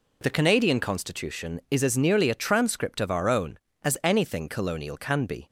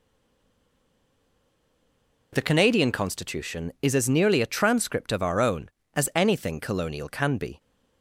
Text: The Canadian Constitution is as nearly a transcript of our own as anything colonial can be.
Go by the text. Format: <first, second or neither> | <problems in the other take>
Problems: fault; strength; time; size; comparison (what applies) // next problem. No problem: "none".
first | stays silent before the first word; until 2.3 s; 2.3 s long